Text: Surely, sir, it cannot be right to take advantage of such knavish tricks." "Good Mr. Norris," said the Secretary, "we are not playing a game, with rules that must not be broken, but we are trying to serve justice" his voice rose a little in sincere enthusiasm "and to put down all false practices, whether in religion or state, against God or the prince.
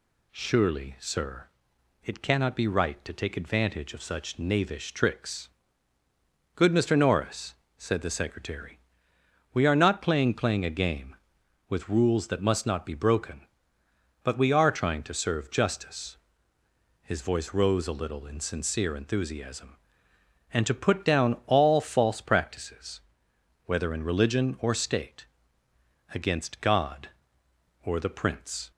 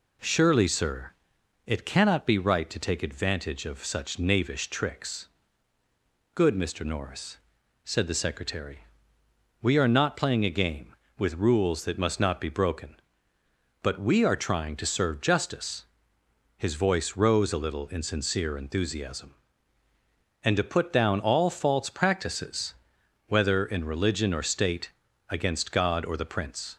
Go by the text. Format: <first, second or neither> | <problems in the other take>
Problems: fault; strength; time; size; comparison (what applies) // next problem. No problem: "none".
second | says "playing" twice; at 10.3 s // pauses between "justice" and "his"; noticeable; at 16.1 s; 0.87 s long; noticeable in the second